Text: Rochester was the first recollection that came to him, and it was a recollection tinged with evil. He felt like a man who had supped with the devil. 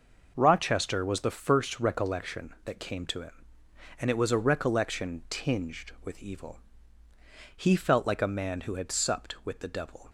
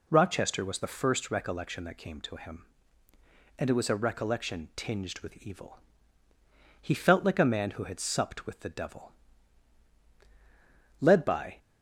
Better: first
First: none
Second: goes on to say "Led by"; from 11.0 s on; 0.56 s long

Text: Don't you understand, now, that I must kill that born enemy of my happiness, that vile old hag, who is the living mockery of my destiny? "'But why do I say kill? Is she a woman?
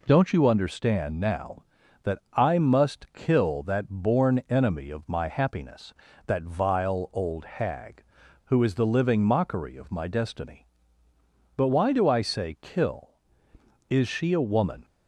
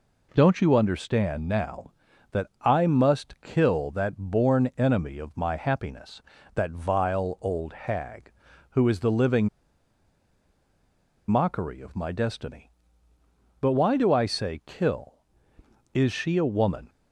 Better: first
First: pauses between "that" and "I"; slight; at 2.1 s; 0.16 s long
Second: pauses between "that" and "I"; slight; at 2.4 s; 0.16 s long // pauses between "living" and "mockery"; strong; at 9.4 s; 1.8 s long

